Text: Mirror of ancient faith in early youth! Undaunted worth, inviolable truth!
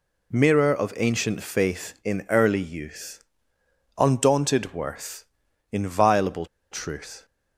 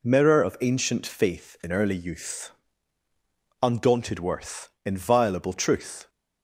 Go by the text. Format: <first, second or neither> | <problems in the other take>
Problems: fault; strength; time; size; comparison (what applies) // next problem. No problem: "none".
second | pauses between "inviolable" and "truth"; slight; at 6.4 s; 0.25 s long